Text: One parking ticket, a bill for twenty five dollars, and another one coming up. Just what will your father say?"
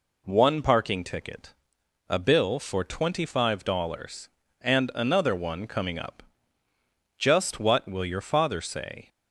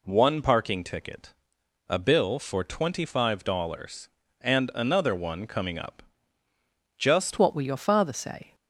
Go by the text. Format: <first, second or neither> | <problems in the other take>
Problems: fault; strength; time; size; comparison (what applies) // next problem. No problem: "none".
first | changes voice at "what"; from 7.3 s on; 1.2 s long